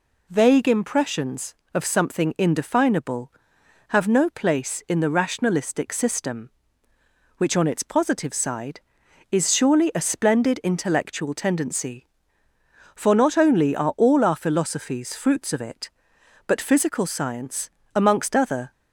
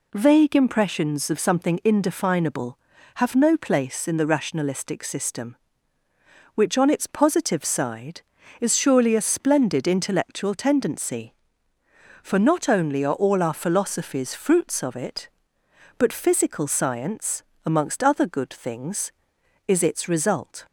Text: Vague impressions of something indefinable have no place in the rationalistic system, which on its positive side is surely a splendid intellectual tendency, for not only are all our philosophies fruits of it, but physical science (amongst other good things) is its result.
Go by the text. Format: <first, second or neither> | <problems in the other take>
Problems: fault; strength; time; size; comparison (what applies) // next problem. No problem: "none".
second | stops before "good things is its result"; at 18.7 s